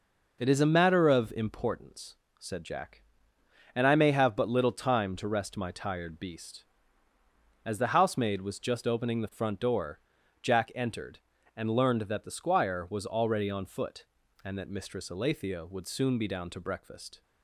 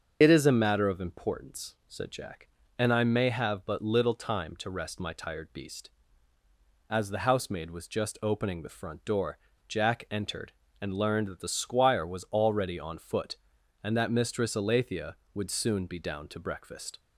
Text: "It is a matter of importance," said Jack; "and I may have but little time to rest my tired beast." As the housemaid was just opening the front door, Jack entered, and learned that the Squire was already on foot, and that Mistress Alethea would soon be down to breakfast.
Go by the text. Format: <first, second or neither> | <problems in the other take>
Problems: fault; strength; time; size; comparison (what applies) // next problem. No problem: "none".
first | loses the start of "It"; at 0.2 s; 60 ms // starts louder than the rest; until 1.2 s; 6.5 dB